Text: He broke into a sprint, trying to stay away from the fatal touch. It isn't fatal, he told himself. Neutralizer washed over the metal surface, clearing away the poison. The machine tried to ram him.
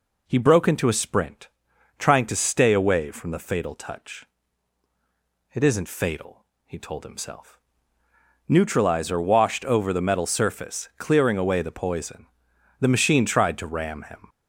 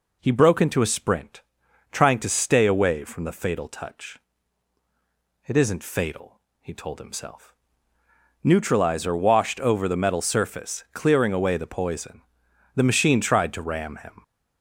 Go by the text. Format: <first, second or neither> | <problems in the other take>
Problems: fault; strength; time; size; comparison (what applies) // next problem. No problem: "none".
neither | none